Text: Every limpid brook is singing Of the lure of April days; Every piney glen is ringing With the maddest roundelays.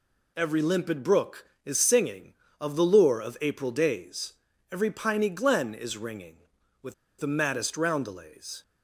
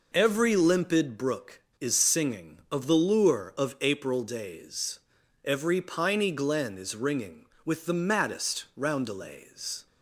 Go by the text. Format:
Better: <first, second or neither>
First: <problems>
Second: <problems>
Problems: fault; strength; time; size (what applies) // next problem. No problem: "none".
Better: second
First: pauses between "With" and "the"; slight; at 6.9 s; 0.24 s long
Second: none